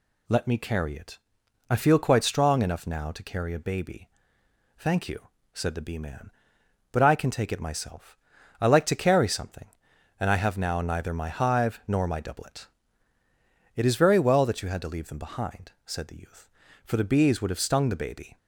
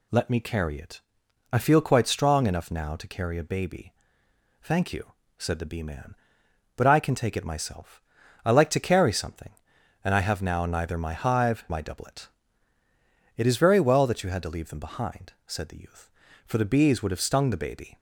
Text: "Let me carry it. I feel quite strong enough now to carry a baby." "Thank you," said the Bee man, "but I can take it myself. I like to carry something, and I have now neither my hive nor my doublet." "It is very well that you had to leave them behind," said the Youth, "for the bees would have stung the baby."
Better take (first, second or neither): first